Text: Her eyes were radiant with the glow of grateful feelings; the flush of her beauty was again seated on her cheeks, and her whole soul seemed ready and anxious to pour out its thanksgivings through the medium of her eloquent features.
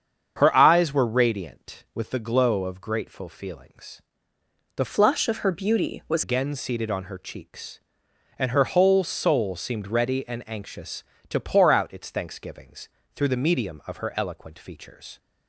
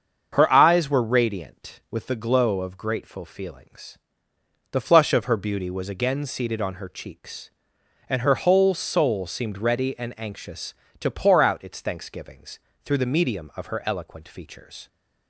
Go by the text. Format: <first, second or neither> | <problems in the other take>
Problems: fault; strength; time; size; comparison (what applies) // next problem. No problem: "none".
second | starts louder than the rest; strong; until 1.3 s; 7.5 dB; also in the second // changes voice from "flush" to "was"; from 4.8 to 6.2 s; 1.4 s long // pauses between "thanksgivings" and "through"; slight; at 12.8 s; 0.28 s long; slight in the second